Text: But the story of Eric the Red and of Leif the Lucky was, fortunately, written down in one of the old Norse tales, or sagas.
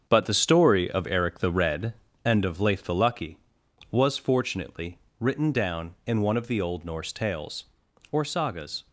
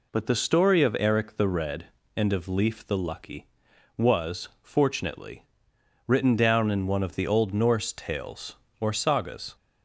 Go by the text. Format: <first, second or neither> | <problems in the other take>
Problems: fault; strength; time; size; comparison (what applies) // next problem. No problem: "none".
second | gets quieter; throughout; 7 dB